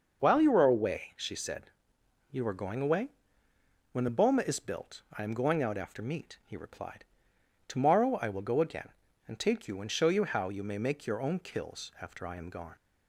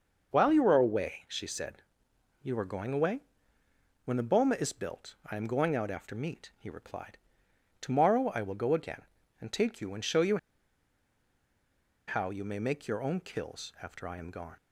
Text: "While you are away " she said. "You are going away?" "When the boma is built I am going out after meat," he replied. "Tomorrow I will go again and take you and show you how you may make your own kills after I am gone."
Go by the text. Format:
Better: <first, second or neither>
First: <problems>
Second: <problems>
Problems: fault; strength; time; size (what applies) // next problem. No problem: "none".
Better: first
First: starts louder than the rest; noticeable; until 1.2 s; 6 dB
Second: starts louder than the rest; noticeable; until 1.3 s; 6 dB // pauses between "you" and "how"; strong; at 10.3 s; 1.6 s long